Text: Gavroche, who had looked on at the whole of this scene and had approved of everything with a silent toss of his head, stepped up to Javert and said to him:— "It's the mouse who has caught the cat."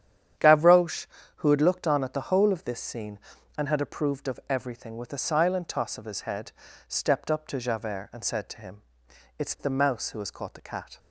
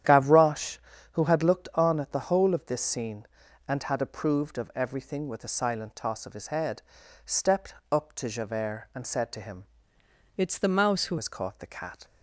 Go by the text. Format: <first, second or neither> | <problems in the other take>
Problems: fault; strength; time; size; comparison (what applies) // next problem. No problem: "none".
first | starts louder than the rest; strong; until 1.4 s; 10 dB; strong in the first // pauses between "stepped" and "up"; slight; at 7.7 s; 0.18 s long // changes voice from "It's" to "who"; from 10.3 to 11.1 s; 0.8 s long